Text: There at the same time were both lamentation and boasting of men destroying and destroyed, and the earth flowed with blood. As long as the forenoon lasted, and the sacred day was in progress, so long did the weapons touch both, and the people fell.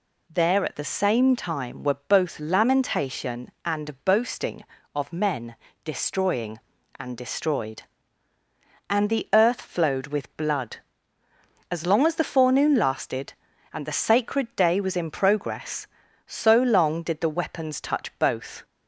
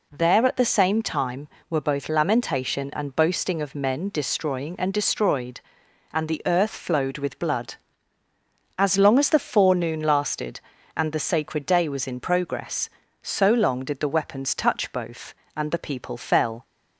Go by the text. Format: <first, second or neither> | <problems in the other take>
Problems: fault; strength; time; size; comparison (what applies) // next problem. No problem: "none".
second | pauses between "men" and "destroying"; slight; at 5.5 s; 0.30 s long // stops before "and the people fell"; at 18.6 s